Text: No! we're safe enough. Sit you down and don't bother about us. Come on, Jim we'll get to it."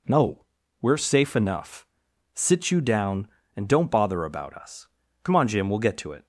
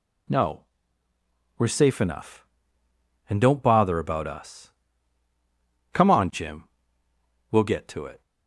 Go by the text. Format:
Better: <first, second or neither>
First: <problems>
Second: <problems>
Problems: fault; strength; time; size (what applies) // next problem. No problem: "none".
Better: first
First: none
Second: skips "Sit you down"; at 2.8 s // pauses between "Jim" and "we'll"; noticeable; at 6.6 s; 0.86 s long